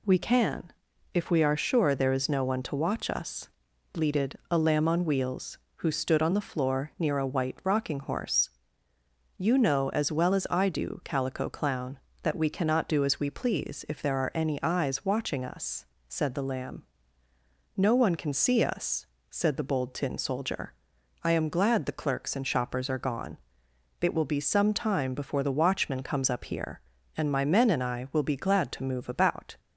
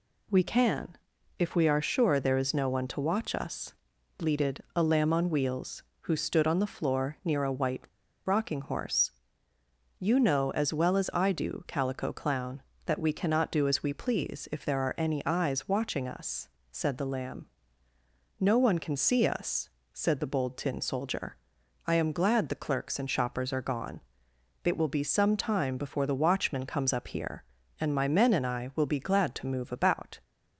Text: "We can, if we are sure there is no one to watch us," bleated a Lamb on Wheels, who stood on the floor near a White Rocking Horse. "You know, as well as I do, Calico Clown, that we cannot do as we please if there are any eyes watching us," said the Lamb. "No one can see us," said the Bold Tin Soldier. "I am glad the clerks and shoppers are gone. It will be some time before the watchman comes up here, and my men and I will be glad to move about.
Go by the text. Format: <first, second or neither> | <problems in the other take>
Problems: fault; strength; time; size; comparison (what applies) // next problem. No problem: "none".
first | pauses between "White" and "Rocking"; at 7.8 s; 0.41 s long